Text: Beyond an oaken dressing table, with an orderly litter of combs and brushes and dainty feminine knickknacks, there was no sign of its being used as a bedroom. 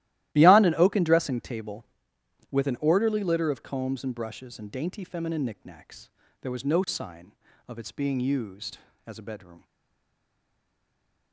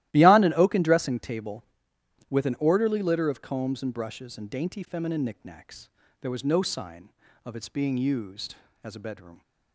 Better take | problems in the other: second | starts louder than the rest; strong; until 1.3 s; 15 dB; strong in the second // stays silent after the last word; noticeable; from 9.6 s on; 1.7 s long

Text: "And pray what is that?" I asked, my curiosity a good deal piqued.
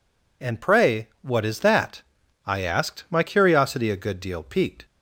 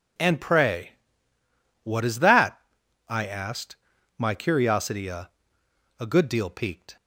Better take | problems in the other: first | pauses between "pray" and "what"; noticeable; at 0.9 s; 0.92 s long // says "a" twice; at 6.0 s

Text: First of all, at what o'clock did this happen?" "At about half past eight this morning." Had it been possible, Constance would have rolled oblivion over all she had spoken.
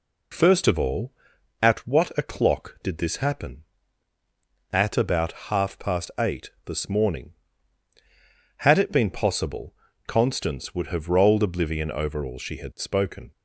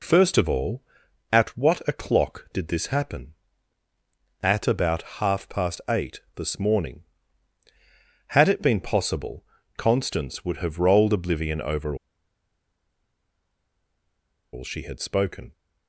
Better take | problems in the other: first | pauses between "about" and "half"; slight; at 5.0 s; 0.18 s long; slight in the first // pauses between "eight" and "this"; slight; at 6.1 s; 0.16 s long; slight in the first // pauses between "over" and "all"; strong; at 11.9 s; 2.5 s long

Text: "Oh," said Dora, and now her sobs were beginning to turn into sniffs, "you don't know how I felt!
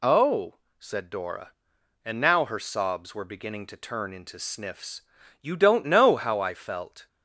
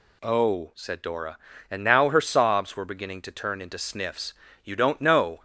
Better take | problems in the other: first | stops before "how I felt"; at 5.3 s

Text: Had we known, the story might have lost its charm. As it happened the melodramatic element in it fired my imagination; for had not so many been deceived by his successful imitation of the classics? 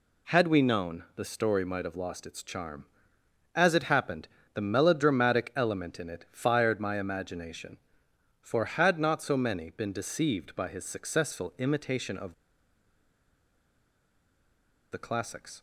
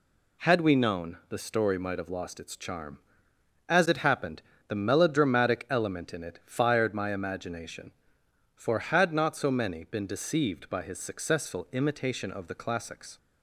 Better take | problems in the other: second | pauses between "happened" and "the"; slight; at 4.2 s; 0.28 s long; slight in the second // pauses between "of" and "the"; strong; at 12.3 s; 2.5 s long

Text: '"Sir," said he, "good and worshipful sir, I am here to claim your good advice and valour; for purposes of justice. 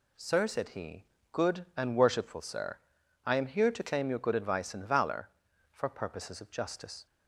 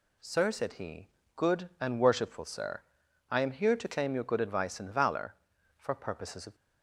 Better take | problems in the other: first | stops before "justice"; at 6.5 s

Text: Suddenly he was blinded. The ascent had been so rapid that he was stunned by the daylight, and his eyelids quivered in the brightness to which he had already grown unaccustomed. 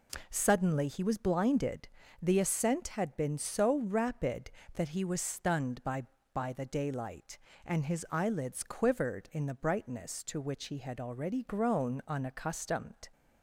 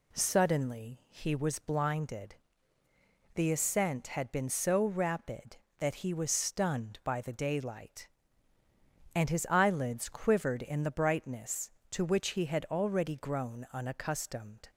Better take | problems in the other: second | says "by" twice; at 6.3 s

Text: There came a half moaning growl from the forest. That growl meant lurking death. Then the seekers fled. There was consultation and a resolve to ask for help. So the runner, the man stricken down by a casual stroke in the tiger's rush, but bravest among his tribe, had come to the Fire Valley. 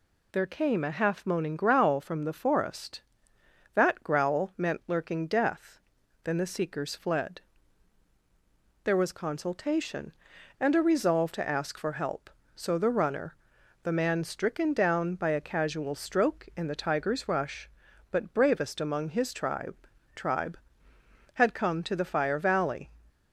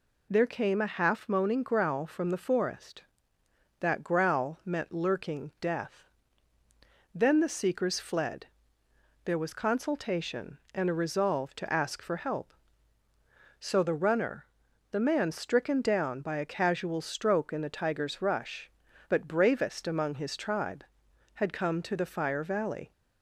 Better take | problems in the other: second | says "tribe" twice; at 20.1 s

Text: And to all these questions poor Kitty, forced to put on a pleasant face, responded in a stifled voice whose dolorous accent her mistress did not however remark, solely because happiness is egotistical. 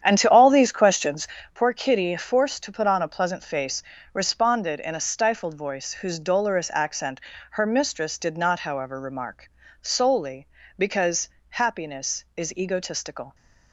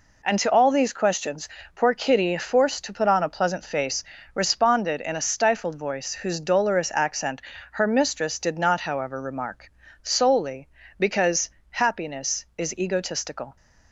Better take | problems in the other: second | starts louder than the rest; strong; until 1.5 s; 9 dB // pauses between "questions" and "poor"; slight; at 1.2 s; 0.26 s long; slight in the second // pauses between "accent" and "her"; slight; at 7.2 s; 0.30 s long; slight in the second // pauses between "because" and "happiness"; slight; at 11.2 s; 0.22 s long; slight in the second

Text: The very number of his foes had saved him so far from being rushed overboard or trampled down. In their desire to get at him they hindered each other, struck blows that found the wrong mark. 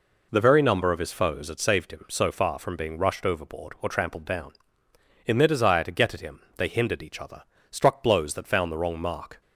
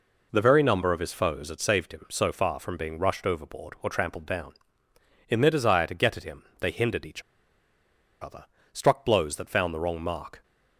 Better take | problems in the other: first | pauses between "him" and "they"; slight; at 6.4 s; 0.16 s long; slight in the first // pauses between "each" and "other"; at 7.2 s; 1.0 s long

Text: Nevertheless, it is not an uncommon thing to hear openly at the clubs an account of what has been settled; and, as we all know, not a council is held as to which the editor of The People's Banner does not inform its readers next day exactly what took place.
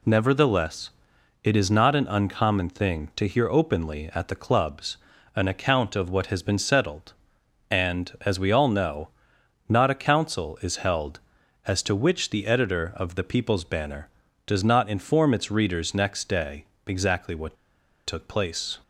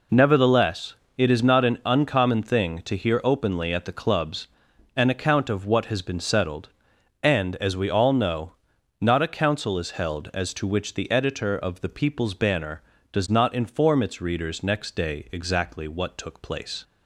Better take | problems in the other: second | pauses between "clubs" and "an"; at 4.9 s; 0.38 s long; noticeable in the second // pauses between "day" and "exactly"; slight; at 16.6 s; 0.22 s long // pauses between "what" and "took"; noticeable; at 17.5 s; 0.51 s long

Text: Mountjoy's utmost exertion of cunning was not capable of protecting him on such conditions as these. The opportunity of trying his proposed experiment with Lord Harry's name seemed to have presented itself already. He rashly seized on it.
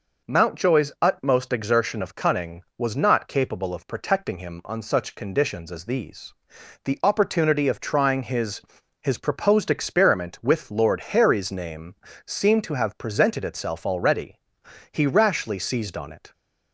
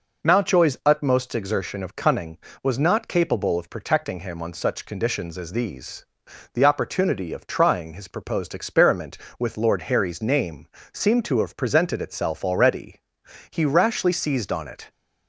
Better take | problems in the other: second | says "his" twice; at 9.0 s // pauses between "name" and "seemed"; slight; at 11.9 s; 0.30 s long; slight in the second

